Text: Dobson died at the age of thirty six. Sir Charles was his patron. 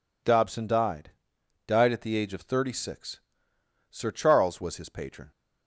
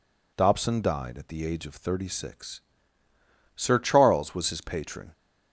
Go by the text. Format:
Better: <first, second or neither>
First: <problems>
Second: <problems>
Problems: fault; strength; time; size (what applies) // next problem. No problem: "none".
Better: second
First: says "died" twice; at 1.6 s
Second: none